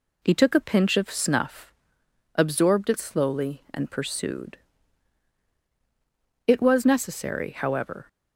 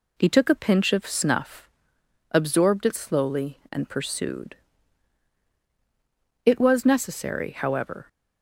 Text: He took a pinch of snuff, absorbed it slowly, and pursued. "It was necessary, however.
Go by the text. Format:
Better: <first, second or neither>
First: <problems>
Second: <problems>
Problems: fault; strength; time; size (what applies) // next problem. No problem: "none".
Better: neither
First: none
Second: none